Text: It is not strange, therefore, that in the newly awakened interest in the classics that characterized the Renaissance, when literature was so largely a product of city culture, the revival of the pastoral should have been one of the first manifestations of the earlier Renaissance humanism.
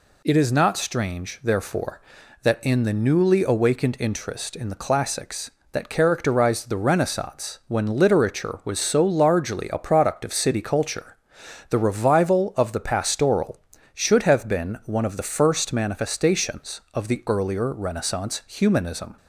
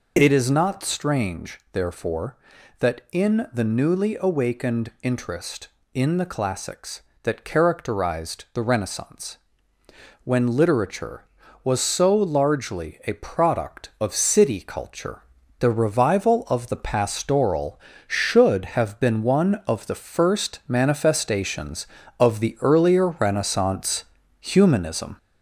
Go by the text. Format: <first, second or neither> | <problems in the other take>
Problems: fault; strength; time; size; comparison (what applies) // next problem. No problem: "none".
first | gets louder; slight; throughout; 2.5 dB // pauses between "Renaissance" and "humanism"; slight; at 24.0 s; 0.36 s long